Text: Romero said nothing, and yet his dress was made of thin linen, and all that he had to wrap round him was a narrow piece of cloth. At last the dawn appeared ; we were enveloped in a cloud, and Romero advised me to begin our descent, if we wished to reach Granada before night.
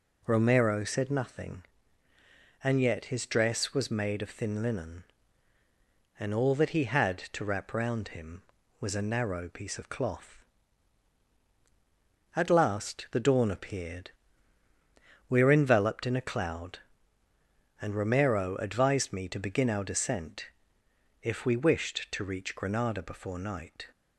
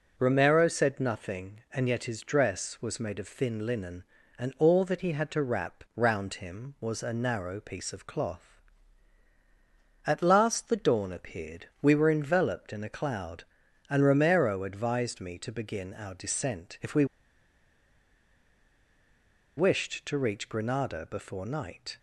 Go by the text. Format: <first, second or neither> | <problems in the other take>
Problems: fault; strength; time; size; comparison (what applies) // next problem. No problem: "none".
first | pauses between "we" and "wished"; strong; at 17.0 s; 2.5 s long